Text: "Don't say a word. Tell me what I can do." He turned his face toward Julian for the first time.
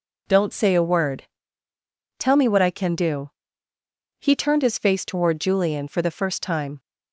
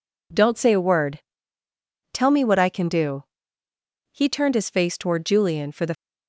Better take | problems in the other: first | stops before "first time"; at 5.9 s

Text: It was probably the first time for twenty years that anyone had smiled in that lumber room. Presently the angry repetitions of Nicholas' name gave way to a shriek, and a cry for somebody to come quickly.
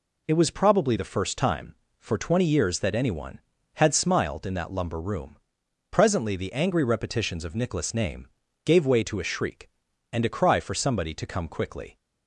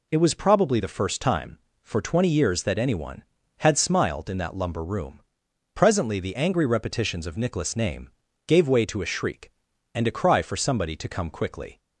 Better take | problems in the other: neither | pauses between "name" and "gave"; the same in both

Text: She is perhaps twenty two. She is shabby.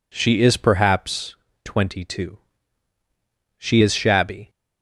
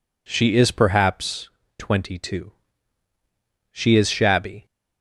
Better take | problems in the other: neither | pauses between "perhaps" and "twenty"; slight; the same in both

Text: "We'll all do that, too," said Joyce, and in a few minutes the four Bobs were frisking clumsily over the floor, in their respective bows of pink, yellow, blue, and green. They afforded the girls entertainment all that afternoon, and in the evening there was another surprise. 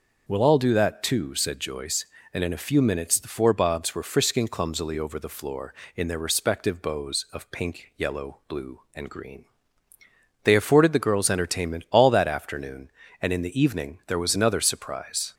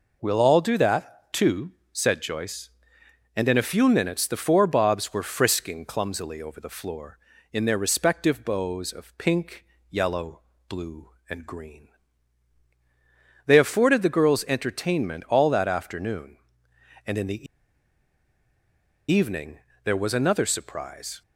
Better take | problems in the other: first | pauses between "the" and "evening"; strong; at 17.4 s; 1.6 s long // pauses between "evening" and "there"; slight; at 19.5 s; 0.24 s long

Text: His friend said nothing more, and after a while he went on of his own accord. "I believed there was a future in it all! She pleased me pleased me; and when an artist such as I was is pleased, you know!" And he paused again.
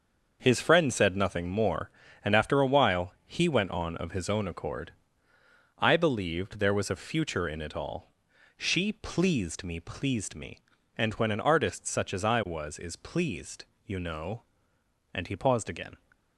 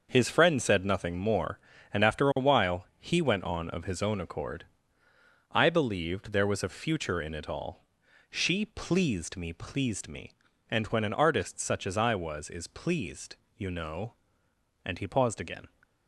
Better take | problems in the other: neither | starts louder than the rest; the same in both

